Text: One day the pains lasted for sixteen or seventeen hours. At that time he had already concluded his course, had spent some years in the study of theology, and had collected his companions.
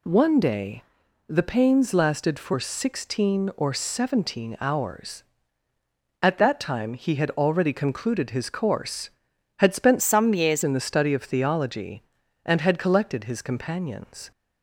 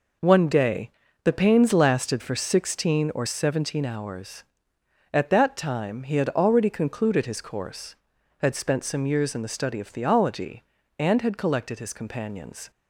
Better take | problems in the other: second | pauses between "day" and "the"; noticeable; at 0.8 s; 0.46 s long; slight in the second // changes voice from "some" to "years"; from 10.0 to 10.6 s; 0.6 s long

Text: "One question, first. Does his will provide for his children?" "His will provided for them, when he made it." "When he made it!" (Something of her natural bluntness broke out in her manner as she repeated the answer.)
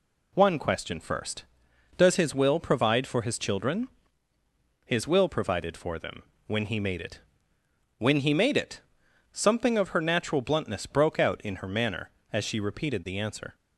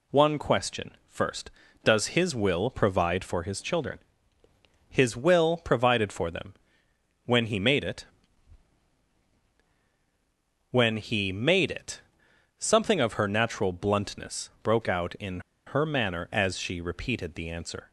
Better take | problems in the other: first | pauses between "bluntness" and "broke"; slight; at 14.4 s; 0.16 s long // pauses between "in" and "her"; slight; at 15.3 s; 0.26 s long

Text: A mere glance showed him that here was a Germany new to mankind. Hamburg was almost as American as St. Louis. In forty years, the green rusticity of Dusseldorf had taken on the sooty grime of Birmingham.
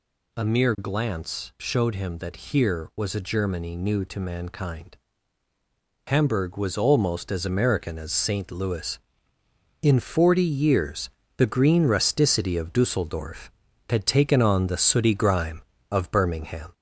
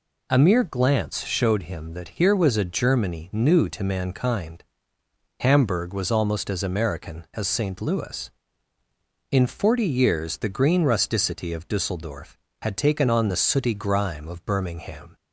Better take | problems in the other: second | gets louder; slight; throughout; 2.5 dB

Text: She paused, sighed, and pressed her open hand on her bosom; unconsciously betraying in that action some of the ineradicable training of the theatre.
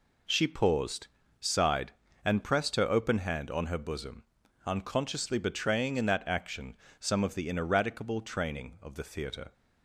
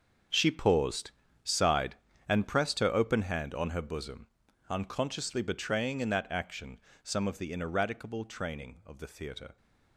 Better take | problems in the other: first | gets quieter; strong; throughout; 13.5 dB // pauses between "action" and "some"; slight; at 6.7 s; 0.24 s long; slight in the first

